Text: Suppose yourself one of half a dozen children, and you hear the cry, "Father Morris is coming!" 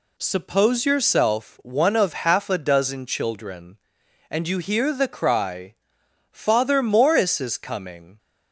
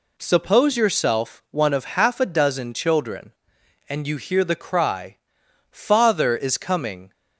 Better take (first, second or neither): first